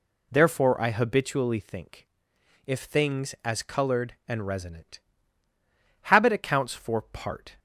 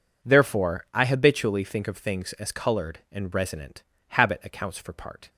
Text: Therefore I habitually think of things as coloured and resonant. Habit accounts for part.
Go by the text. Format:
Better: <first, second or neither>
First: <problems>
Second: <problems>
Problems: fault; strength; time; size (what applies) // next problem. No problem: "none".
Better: second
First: says "if" for "of"; at 2.6 s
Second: none